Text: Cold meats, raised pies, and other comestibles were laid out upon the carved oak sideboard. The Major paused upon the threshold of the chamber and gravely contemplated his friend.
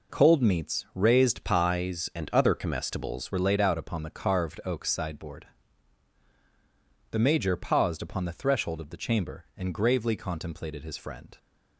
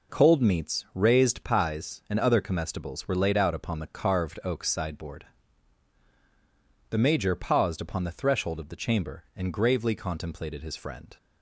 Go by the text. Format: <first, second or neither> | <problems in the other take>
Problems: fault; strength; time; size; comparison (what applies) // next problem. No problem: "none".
second | changes voice from "pies" to "comestibles"; from 1.4 to 3.3 s; 1.9 s long